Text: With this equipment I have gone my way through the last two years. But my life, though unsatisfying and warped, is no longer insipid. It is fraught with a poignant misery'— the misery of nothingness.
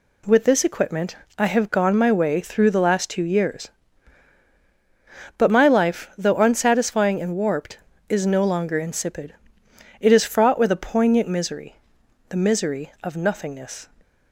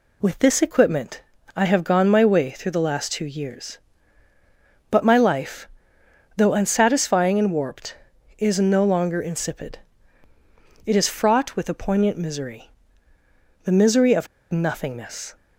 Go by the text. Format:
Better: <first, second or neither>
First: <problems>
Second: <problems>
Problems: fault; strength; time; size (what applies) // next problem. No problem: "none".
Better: first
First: pauses between "equipment" and "I"; slight; at 1.1 s; 0.20 s long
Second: pauses between "equipment" and "I"; slight; at 1.2 s; 0.32 s long // pauses between "of" and "nothingness"; slight; at 14.2 s; 0.24 s long